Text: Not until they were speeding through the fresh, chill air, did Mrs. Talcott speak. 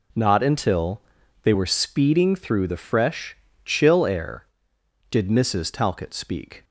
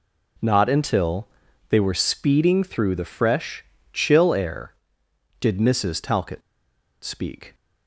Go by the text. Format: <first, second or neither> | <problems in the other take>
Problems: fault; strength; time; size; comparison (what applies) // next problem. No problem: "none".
first | pauses between "until" and "they"; at 1.2 s; 0.42 s long; also in the first // pauses between "Talcott" and "speak"; noticeable; at 6.4 s; 0.63 s long